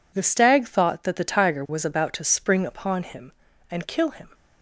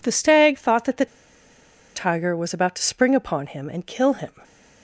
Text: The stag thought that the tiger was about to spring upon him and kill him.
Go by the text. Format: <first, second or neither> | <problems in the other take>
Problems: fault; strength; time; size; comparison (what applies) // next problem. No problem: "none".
first | pauses between "the" and "tiger"; noticeable; at 1.0 s; 0.89 s long // stays silent after the last word; slight; from 4.2 s on; 0.6 s long